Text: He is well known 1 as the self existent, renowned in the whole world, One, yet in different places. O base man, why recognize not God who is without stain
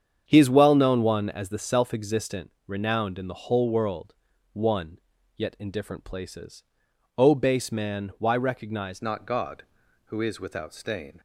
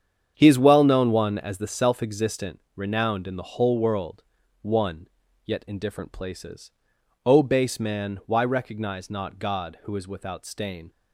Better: second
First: starts louder than the rest; strong; until 1.2 s; 8 dB // changes voice at "not"; from 9.0 s on; 2.1 s long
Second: starts louder than the rest; strong; until 1.3 s; 8 dB

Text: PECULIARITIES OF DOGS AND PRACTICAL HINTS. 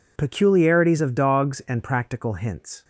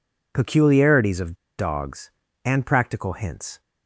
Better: first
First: none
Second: pauses between "OF" and "DOGS"; slight; at 1.3 s; 0.24 s long

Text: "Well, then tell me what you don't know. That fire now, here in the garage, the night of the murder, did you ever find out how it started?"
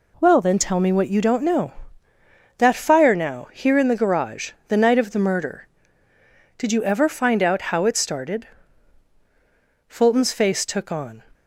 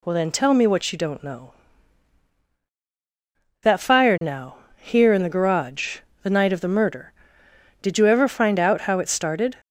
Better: second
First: goes on to say "Fulton's face took on"; from 9.8 s on; 1.3 s long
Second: none

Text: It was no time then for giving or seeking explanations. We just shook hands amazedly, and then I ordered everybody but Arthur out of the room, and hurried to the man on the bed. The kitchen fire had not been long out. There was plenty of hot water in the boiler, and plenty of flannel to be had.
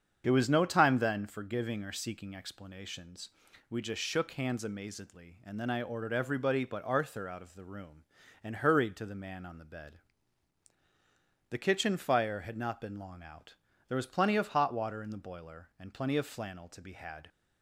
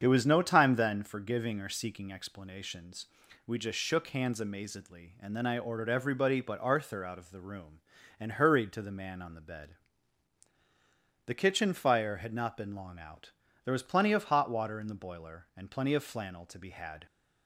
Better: neither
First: starts louder than the rest; strong; until 1.2 s; 7.5 dB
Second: starts louder than the rest; strong; until 1.0 s; 7.5 dB

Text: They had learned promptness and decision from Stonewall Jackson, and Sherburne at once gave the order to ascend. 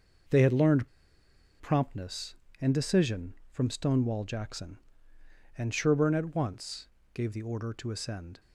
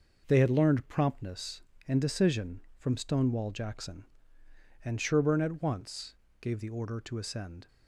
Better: second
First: pauses between "learned" and "promptness"; noticeable; at 0.8 s; 0.72 s long // pauses between "once" and "gave"; slight; at 6.8 s; 0.26 s long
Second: pauses between "once" and "gave"; slight; at 6.1 s; 0.26 s long

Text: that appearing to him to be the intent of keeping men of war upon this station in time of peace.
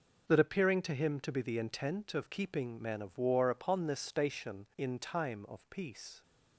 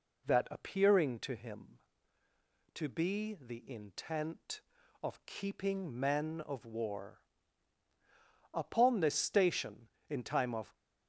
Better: first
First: none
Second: pauses between "war" and "upon"; strong; at 7.1 s; 1.3 s long // stops before "peace"; at 10.7 s

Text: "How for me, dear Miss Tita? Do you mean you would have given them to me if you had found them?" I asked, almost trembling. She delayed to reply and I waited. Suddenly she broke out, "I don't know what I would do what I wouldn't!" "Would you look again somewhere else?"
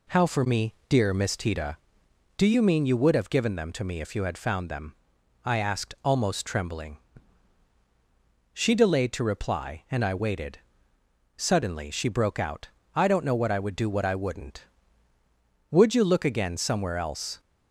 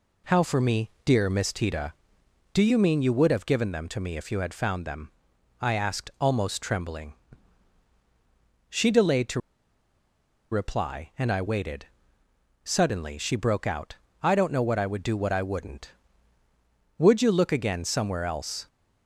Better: first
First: none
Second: pauses between "to" and "reply"; at 9.3 s; 1.1 s long

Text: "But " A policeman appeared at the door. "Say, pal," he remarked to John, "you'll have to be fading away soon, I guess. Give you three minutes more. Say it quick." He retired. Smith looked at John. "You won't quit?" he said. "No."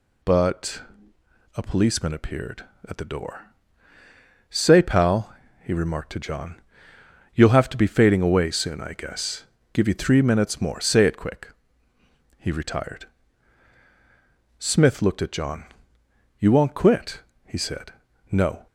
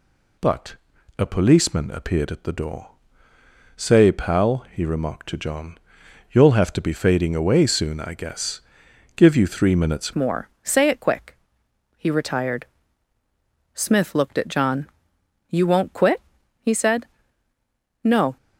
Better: first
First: none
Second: changes voice at "more"; from 10.1 s on; 8.2 s long

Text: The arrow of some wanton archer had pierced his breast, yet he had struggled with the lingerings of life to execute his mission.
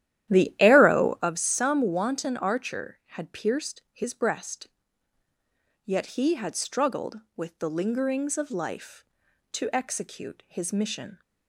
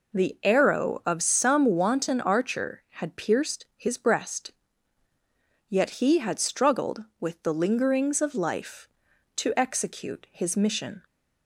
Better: second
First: starts louder than the rest; strong; until 1.4 s; 12 dB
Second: none

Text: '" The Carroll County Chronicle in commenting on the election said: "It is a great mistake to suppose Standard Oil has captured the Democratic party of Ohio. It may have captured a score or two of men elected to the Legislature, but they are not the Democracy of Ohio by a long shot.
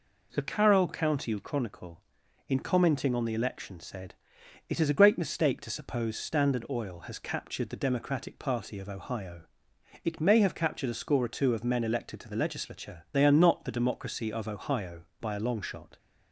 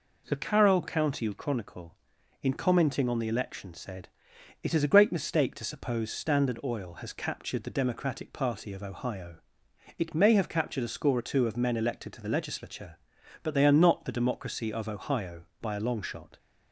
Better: second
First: skips "but"; at 13.0 s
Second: none

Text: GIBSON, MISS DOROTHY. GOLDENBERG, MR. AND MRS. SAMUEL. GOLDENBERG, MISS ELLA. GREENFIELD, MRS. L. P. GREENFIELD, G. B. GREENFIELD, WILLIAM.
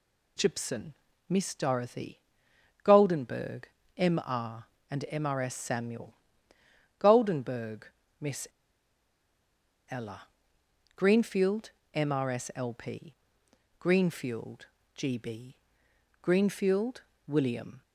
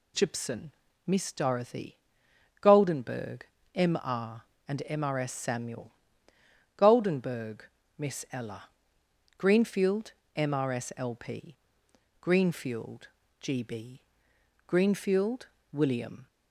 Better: second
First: pauses between "MISS" and "ELLA"; strong; at 8.4 s; 1.4 s long // pauses between "P" and "GREENFIELD"; noticeable; at 13.1 s; 0.64 s long // pauses between "B" and "GREENFIELD"; noticeable; at 15.5 s; 0.64 s long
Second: pauses between "P" and "GREENFIELD"; noticeable; at 11.5 s; 0.64 s long // pauses between "B" and "GREENFIELD"; noticeable; at 14.0 s; 0.64 s long

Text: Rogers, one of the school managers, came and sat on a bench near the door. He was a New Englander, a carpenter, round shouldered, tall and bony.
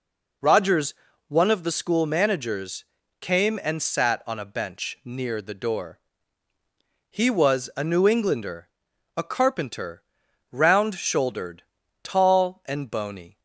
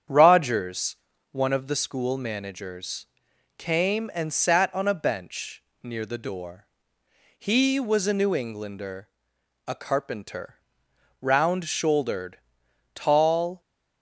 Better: first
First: none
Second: starts louder than the rest; strong; until 1.4 s; 8.5 dB // pauses between "bench" and "near"; slight; at 5.6 s; 0.22 s long // stops before "and bony"; at 13.6 s

